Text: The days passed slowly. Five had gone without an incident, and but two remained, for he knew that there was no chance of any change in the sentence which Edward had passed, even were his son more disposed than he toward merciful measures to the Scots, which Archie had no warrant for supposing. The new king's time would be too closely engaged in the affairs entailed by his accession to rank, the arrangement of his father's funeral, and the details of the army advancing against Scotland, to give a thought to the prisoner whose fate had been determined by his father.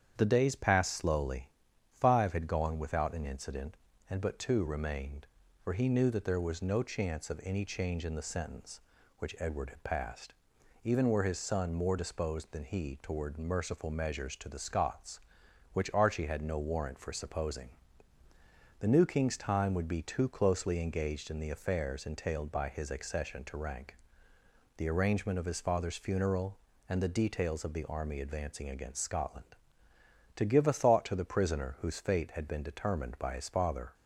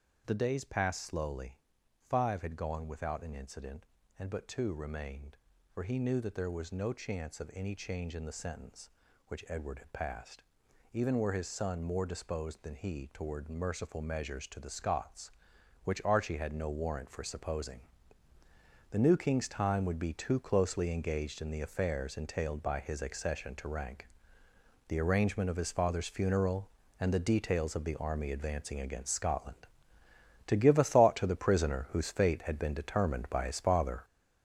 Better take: first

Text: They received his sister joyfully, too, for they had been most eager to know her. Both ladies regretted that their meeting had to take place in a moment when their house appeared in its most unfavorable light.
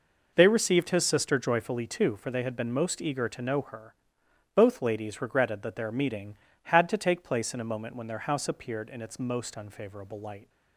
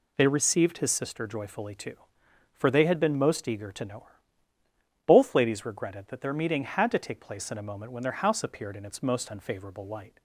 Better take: neither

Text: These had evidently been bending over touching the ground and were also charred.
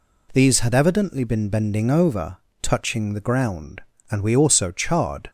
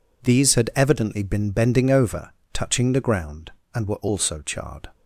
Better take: second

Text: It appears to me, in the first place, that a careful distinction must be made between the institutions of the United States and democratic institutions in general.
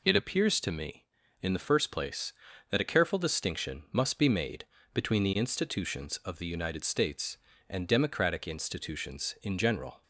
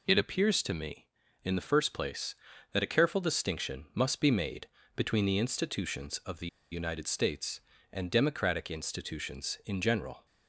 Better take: first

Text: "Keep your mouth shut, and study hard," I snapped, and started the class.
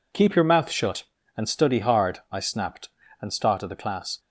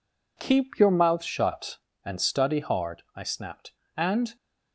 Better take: first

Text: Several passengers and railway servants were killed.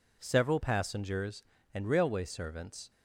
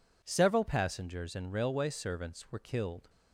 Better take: second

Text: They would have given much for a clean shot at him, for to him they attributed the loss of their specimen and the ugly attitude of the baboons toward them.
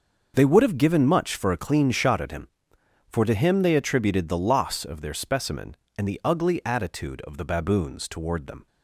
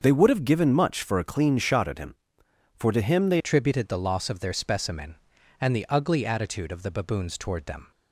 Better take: first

